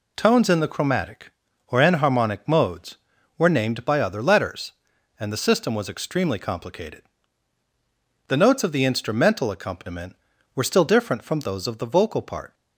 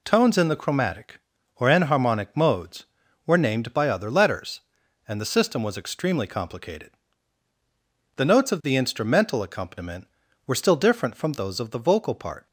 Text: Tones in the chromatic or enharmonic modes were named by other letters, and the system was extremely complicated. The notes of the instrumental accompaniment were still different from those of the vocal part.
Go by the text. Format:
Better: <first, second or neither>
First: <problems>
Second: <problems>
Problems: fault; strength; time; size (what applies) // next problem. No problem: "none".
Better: neither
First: none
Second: none